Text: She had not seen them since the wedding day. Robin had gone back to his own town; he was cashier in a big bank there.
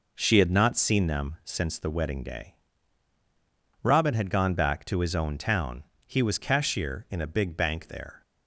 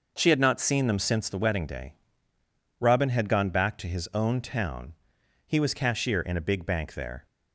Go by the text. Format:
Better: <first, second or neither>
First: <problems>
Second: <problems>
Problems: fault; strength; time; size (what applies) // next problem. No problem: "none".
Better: neither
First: none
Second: none